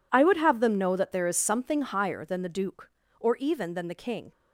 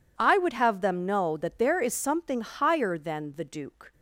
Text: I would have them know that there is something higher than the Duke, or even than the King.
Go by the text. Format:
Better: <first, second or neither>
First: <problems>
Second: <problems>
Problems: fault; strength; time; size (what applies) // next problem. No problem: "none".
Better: first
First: none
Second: stops before "or even than the King"; at 3.9 s